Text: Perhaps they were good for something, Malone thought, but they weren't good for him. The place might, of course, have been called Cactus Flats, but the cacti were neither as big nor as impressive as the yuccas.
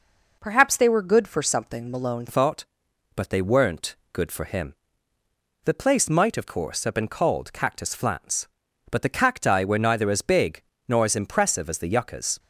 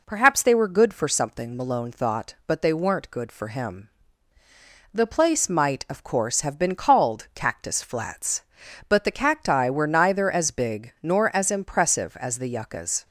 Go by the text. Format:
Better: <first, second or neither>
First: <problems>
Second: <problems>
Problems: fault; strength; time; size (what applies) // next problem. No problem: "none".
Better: second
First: changes voice at "thought"; from 2.2 s on; 10.1 s long // pauses between "weren't" and "good"; slight; at 3.9 s; 0.18 s long // pauses between "big" and "nor"; slight; at 10.6 s; 0.28 s long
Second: none